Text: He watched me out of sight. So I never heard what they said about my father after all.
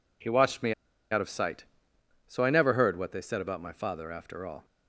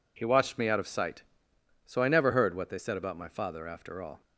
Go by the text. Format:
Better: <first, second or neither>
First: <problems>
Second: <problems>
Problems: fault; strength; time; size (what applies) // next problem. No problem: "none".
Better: second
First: pauses between "me" and "out"; at 0.7 s; 0.39 s long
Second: none